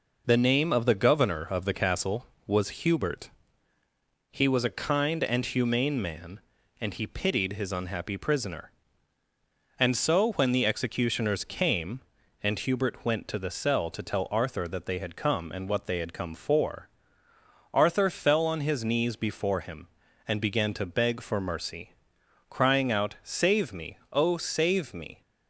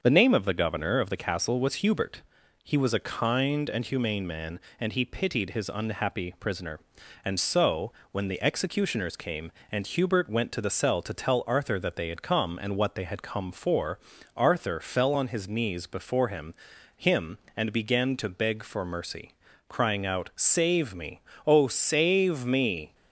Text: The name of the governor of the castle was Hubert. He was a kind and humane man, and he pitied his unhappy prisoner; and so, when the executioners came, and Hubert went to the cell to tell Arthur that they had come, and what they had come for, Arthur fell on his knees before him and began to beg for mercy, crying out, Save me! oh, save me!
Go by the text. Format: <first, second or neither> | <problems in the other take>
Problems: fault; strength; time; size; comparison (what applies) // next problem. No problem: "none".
first | starts louder than the rest; until 1.0 s; 6.5 dB // says "him" twice; at 16.9 s